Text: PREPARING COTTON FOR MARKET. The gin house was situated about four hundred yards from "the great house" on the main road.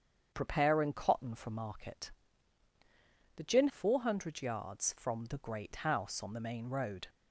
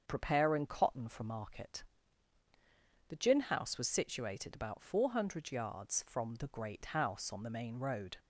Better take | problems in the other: second | starts louder than the rest; strong; until 1.3 s; 7.5 dB; also in the second // skips "house was situated about"; at 3.6 s

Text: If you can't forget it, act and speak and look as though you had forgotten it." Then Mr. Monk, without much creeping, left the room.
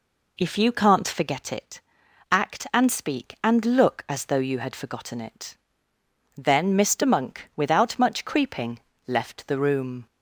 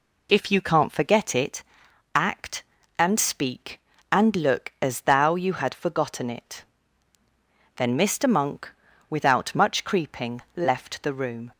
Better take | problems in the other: first | says "thou" for "though"; at 5.0 s

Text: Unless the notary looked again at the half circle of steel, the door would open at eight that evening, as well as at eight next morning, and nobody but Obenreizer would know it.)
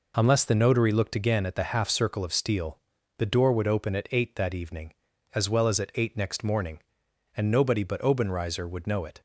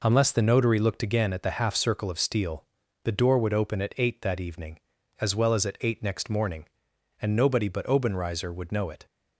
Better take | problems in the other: neither | none

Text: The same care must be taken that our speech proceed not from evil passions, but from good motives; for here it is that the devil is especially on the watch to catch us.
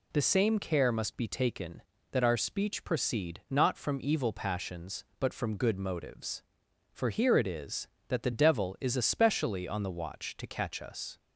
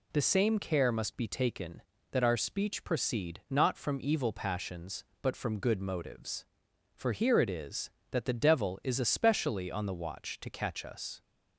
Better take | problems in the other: neither | none

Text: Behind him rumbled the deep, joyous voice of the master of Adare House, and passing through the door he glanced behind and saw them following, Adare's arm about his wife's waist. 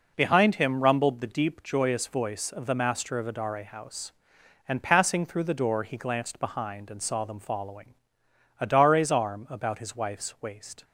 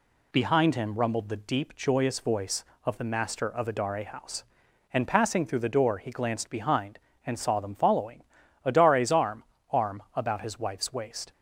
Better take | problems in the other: first | says "arm" twice; at 9.6 s

